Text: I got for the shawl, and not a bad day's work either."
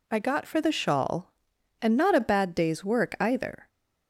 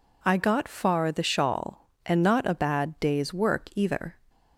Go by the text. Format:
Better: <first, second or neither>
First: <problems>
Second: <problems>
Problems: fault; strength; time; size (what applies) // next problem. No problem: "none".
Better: first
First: none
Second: says "far" for "for"; at 0.6 s